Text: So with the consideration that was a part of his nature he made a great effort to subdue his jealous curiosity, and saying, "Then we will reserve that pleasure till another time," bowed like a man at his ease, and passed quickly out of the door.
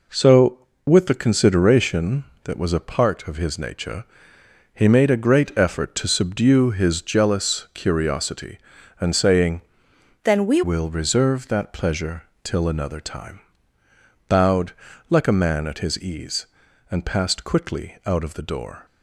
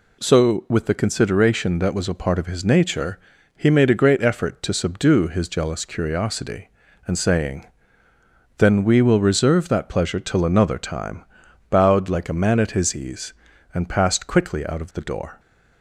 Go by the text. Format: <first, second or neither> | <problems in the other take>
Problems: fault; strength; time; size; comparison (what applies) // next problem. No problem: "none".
second | pauses between "nature" and "he"; noticeable; at 4.0 s; 0.70 s long; also in the second // changes voice from "Then" to "we"; from 10.2 to 10.6 s; 0.4 s long // pauses between "pleasure" and "till"; slight; at 12.2 s; 0.18 s long // pauses between "bowed" and "like"; at 14.7 s; 0.38 s long